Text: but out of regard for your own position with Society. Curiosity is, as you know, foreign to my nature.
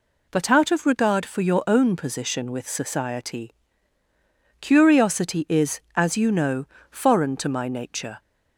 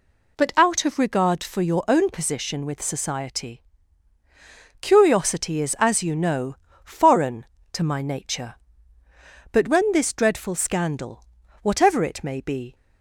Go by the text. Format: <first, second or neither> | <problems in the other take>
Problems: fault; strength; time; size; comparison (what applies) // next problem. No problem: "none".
first | goes on to say "But when this dreadful scandal whatever it may be"; strong; from 9.5 s on; 3.2 s long